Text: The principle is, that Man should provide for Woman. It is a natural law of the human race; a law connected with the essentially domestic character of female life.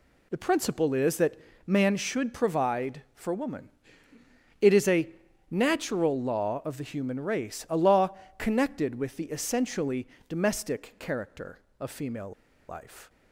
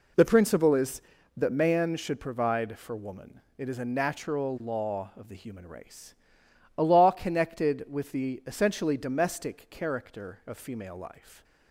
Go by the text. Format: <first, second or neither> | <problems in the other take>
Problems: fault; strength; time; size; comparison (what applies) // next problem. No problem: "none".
second | pauses between "that" and "Man"; slight; at 1.3 s; 0.32 s long // pauses between "a" and "natural"; at 5.0 s; 0.44 s long // pauses between "law" and "connected"; slight; at 8.1 s; 0.22 s long // pauses between "essentially" and "domestic"; slight; at 10.0 s; 0.22 s long // pauses between "female" and "life"; at 12.3 s; 0.37 s long